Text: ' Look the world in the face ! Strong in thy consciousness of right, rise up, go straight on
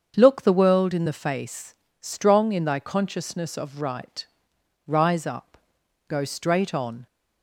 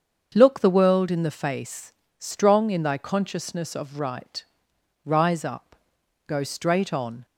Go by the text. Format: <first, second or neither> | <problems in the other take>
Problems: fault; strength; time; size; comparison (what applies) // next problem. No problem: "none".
neither | starts louder than the rest; the same in both